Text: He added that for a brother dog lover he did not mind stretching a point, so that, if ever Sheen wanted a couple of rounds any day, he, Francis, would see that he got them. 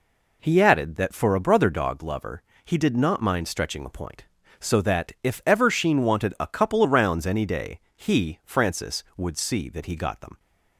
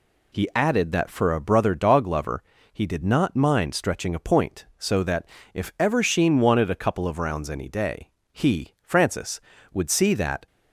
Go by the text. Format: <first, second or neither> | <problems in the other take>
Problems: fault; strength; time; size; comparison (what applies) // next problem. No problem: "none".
first | pauses between "lover" and "he"; slight; at 2.4 s; 0.34 s long; slight in the first // stops before "he got them"; at 10.4 s